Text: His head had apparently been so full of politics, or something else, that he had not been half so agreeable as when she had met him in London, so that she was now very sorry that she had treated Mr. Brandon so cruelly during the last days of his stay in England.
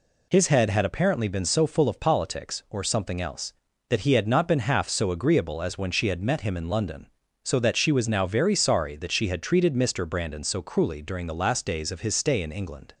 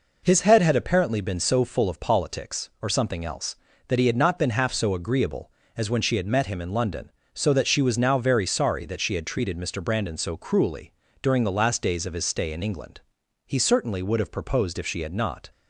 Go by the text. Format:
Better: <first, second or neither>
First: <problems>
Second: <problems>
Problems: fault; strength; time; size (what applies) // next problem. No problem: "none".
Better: first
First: none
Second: pauses between "cruelly" and "during"; slight; at 10.9 s; 0.28 s long // goes on to say "He certainly would have proposed if she had not"; strong; from 13.4 s on; 2.0 s long